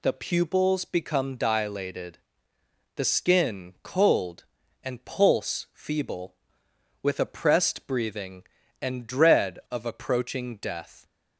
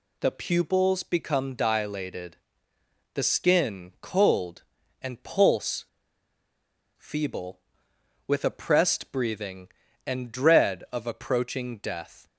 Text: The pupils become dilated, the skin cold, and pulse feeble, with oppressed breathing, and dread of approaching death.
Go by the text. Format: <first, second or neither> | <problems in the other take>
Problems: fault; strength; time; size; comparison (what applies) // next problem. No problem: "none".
first | pauses between "pulse" and "feeble"; at 5.8 s; 1.1 s long